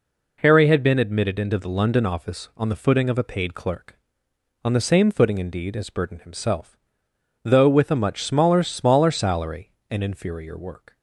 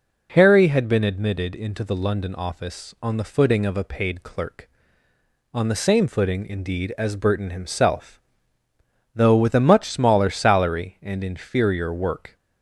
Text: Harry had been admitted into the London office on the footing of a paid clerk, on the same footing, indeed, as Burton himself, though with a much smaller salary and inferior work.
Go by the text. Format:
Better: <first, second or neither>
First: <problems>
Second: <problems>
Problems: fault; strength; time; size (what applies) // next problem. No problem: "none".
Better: second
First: says "smaller" twice; at 8.6 s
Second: none